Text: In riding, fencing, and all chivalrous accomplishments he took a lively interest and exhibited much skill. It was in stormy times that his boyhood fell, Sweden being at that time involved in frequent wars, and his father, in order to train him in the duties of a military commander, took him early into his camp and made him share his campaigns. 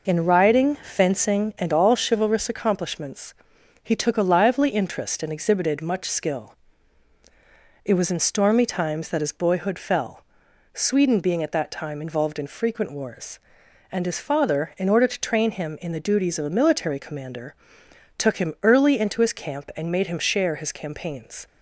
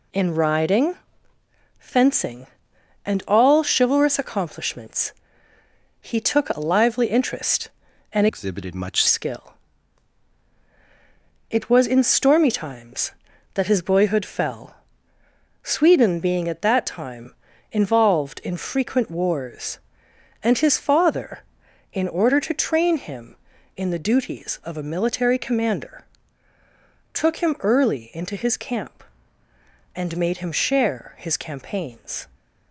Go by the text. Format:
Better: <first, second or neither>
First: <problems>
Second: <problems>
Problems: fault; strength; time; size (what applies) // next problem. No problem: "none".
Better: first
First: pauses between "accomplishments" and "he"; noticeable; at 3.3 s; 0.48 s long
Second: pauses between "accomplishments" and "he"; noticeable; at 5.1 s; 0.88 s long // changes voice from "exhibited" to "much"; from 8.2 to 9.0 s; 0.8 s long // pauses between "time" and "involved"; at 17.3 s; 0.40 s long